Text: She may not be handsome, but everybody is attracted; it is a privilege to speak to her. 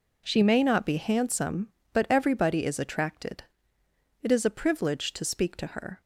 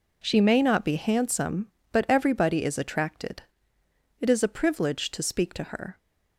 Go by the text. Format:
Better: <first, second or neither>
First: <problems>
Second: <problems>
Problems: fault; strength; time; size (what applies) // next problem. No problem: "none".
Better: neither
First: none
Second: none